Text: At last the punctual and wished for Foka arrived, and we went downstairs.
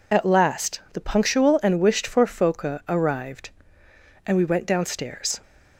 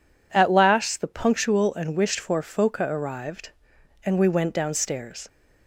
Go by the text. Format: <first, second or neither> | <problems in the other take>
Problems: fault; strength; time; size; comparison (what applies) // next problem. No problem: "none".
second | loses the start of "At"; at 0.1 s; 35 ms